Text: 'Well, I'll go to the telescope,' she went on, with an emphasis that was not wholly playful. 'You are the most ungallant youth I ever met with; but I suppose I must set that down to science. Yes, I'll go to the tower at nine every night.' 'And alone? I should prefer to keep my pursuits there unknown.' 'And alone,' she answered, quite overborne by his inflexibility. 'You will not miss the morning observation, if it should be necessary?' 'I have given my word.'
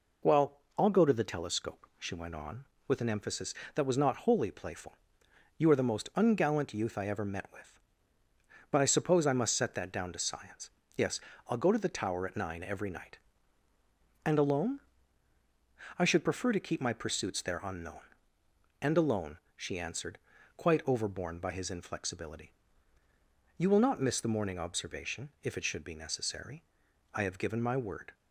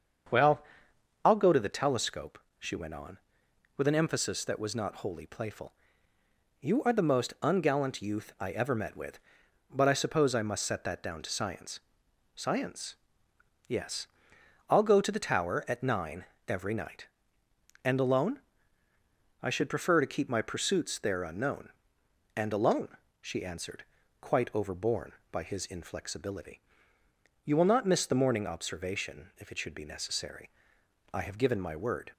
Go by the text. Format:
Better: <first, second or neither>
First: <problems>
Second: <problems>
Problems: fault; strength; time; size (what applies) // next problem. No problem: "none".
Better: first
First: none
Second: starts louder than the rest; strong; until 1.9 s; 7 dB // says "science" twice; at 12.3 s // pauses between "nine" and "every"; slight; at 16.2 s; 0.24 s long